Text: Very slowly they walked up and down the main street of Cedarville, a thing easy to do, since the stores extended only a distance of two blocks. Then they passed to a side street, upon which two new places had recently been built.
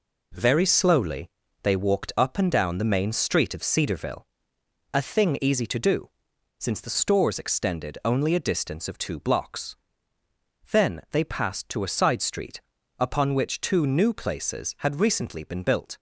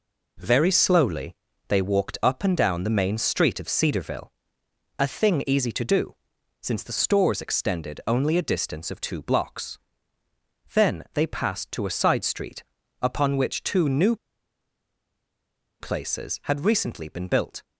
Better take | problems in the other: first | pauses between "slowly" and "they"; slight; at 1.3 s; 0.36 s long; slight in the first // pauses between "new" and "places"; strong; at 14.1 s; 1.6 s long

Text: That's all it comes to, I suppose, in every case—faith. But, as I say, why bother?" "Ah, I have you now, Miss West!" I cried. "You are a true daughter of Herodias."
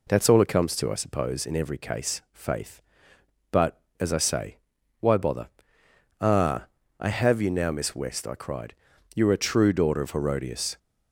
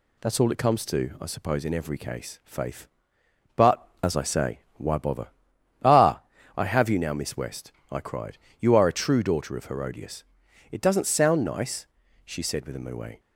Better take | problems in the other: first | goes on to say "It doesn't sound nice she said with a moue"; strong; from 10.7 s on; 2.4 s long

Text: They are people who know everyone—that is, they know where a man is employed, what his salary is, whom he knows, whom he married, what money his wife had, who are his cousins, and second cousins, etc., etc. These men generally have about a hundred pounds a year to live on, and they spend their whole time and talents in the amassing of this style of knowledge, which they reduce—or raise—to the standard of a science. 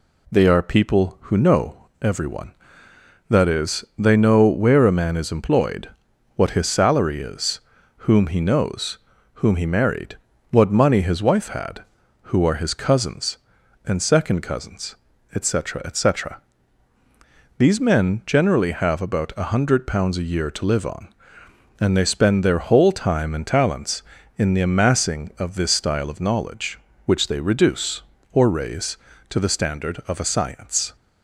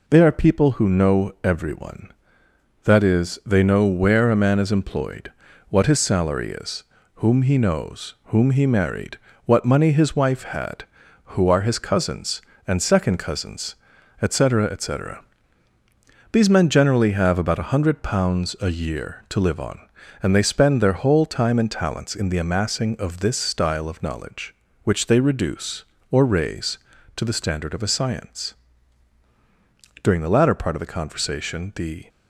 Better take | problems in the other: first | goes on to say "During the latter part of the conversation the"; strong; from 30.0 s on; 2.0 s long

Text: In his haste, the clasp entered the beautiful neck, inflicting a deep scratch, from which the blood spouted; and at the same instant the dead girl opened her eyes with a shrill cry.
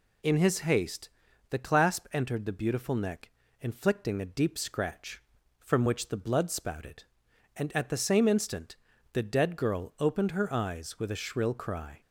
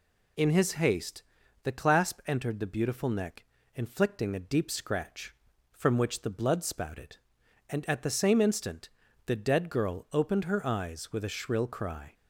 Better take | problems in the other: neither | pauses between "instant" and "the"; slight; the same in both

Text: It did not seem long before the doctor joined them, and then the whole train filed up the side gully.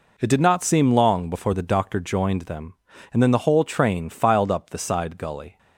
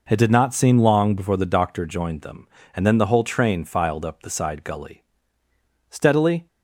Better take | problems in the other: first | goes on to say "Steadily"; from 5.9 s on; 0.56 s long

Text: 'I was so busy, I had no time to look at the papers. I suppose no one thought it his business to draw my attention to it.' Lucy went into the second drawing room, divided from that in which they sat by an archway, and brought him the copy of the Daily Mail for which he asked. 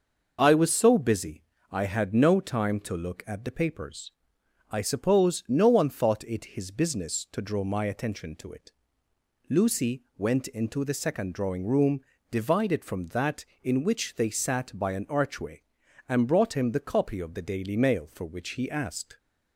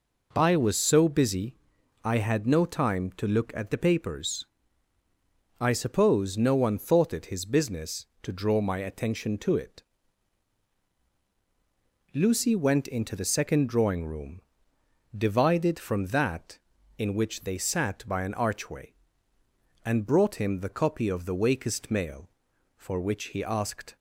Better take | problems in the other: first | says "Wakest" for "Daily"; at 21.3 s

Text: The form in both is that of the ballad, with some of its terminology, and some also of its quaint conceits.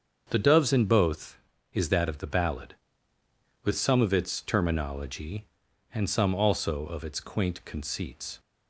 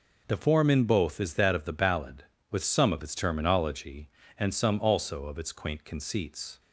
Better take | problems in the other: second | starts louder than the rest; until 1.3 s; 7 dB // says "doves" for "form"; at 0.3 s

